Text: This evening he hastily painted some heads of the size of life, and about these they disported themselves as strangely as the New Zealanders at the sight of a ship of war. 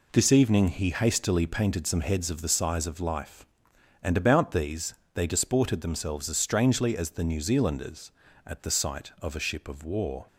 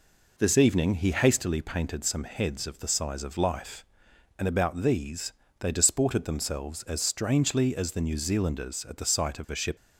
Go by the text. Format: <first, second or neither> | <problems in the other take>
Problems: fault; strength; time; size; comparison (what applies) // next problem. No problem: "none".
first | pauses between "these" and "they"; slight; at 5.3 s; 0.28 s long; slight in the first // stops before "of war"; at 9.7 s